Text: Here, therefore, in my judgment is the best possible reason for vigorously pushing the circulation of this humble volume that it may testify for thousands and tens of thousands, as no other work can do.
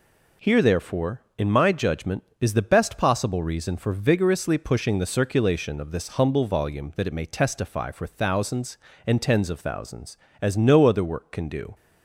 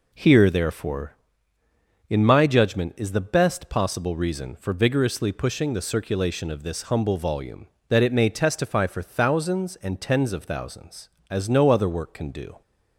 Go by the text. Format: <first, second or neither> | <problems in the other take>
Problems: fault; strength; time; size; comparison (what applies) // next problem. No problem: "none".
neither | none